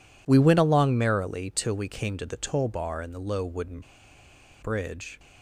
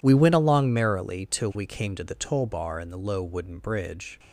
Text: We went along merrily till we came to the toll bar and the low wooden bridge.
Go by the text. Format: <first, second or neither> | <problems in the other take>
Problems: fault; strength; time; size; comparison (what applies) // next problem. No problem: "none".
second | pauses between "wooden" and "bridge"; noticeable; at 3.8 s; 0.81 s long